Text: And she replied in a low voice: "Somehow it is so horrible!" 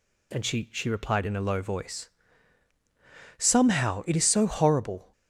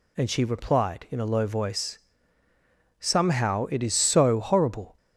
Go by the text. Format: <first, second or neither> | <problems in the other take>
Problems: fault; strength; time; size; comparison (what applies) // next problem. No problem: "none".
second | says "she" twice; at 0.7 s